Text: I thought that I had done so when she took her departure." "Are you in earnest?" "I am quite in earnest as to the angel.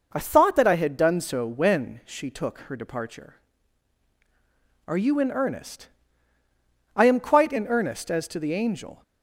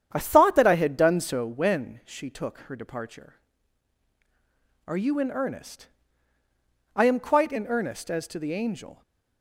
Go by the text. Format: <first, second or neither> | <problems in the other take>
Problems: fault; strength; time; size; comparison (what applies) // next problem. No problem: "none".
first | starts louder than the rest; strong; until 1.6 s; 9 dB